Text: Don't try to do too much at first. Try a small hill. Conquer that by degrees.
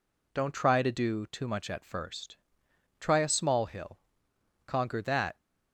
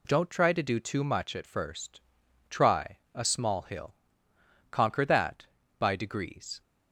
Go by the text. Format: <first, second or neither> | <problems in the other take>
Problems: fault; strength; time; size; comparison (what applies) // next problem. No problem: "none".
second | stops before "by degrees"; at 5.3 s